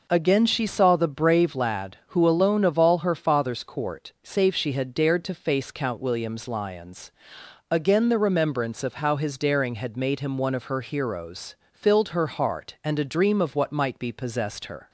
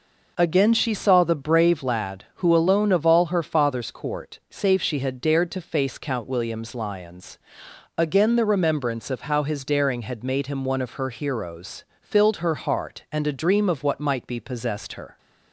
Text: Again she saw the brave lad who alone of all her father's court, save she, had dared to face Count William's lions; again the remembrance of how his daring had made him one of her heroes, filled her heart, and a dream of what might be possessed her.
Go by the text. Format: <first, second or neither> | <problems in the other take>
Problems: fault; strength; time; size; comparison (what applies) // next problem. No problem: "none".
neither | none